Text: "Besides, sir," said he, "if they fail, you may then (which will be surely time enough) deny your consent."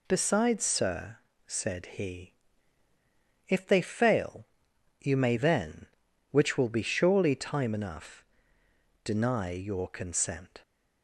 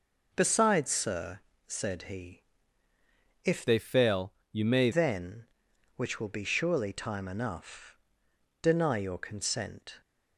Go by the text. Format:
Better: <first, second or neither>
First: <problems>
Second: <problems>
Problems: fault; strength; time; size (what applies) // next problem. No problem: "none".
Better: first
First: none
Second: changes voice from "they" to "may"; from 3.6 to 4.8 s; 1.2 s long